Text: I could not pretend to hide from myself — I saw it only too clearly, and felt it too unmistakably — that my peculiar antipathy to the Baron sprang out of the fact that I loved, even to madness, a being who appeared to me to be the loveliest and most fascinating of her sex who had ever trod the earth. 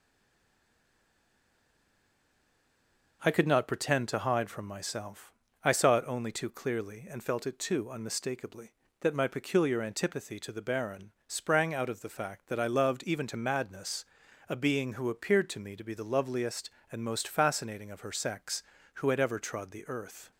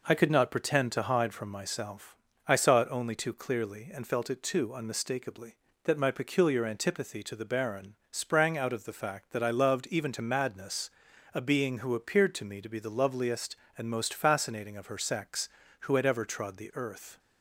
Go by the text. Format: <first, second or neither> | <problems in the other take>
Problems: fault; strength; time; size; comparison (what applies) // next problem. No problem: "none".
second | stays silent before the first word; strong; until 3.2 s; 3.2 s long // pauses between "Baron" and "sprang"; slight; at 11.1 s; 0.16 s long; slight in the second